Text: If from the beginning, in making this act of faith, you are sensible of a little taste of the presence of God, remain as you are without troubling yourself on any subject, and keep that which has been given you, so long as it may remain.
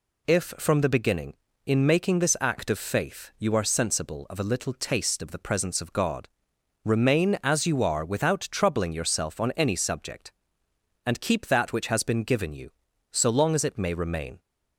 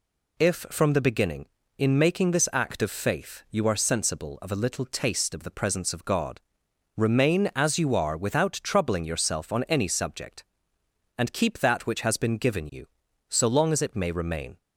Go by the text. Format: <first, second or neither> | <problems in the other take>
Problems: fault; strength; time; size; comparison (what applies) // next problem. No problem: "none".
neither | none